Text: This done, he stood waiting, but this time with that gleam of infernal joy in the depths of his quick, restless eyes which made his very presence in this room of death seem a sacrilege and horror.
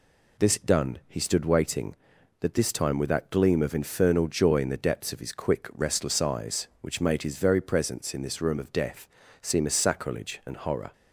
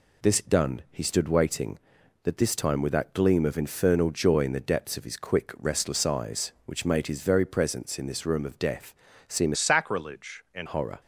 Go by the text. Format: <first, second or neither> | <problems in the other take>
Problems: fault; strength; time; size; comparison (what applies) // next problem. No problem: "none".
first | pauses between "death" and "seem"; slight; at 8.9 s; 0.34 s long; slight in the first // changes voice from "sacrilege" to "and"; from 9.5 to 10.6 s; 1.1 s long